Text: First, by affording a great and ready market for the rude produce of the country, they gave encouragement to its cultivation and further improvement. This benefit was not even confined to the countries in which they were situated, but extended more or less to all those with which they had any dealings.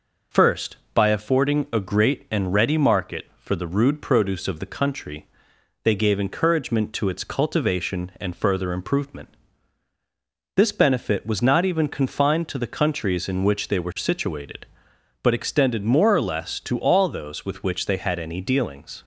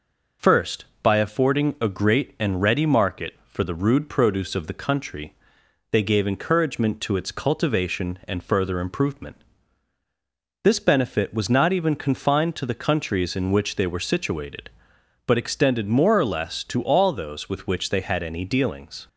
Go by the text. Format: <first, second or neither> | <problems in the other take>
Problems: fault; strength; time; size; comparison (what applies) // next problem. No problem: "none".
neither | none